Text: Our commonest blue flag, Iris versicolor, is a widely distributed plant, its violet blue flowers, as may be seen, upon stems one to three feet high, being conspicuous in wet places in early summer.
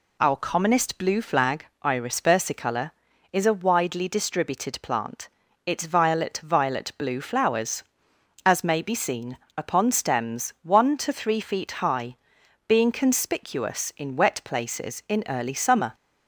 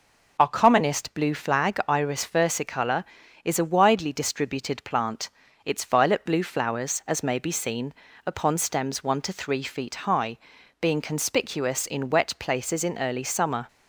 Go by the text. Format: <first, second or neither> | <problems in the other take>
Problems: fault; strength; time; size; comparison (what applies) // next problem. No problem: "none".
second | says "violet" twice; at 6.4 s